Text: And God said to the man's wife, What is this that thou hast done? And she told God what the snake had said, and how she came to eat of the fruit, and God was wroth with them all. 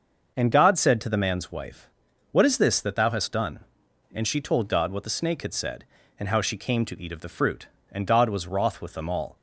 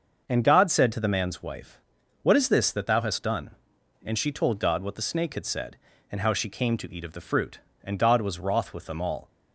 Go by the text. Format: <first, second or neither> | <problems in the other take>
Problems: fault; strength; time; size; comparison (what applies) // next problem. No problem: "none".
neither | starts louder than the rest; the same in both